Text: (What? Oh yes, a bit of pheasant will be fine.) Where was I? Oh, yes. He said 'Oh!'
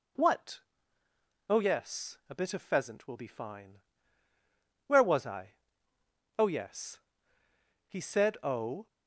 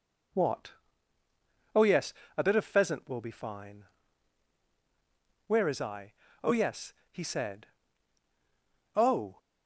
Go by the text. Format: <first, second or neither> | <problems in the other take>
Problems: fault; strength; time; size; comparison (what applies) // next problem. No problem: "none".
first | says "is" for "was"; at 5.6 s // pauses between "said" and "Oh"; strong; at 7.6 s; 1.2 s long